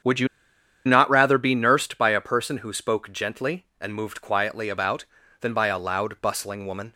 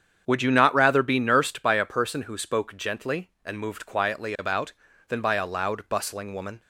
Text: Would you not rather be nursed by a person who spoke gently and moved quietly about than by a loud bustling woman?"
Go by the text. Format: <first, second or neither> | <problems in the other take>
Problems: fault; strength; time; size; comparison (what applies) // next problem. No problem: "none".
second | starts louder than the rest; strong; until 1.6 s; 8 dB; strong in the second // pauses between "you" and "not"; noticeable; at 0.2 s; 0.59 s long